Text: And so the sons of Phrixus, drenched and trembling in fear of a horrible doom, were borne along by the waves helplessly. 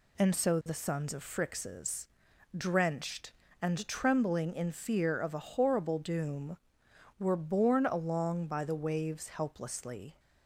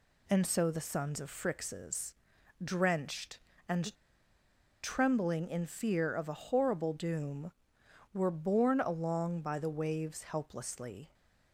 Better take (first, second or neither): first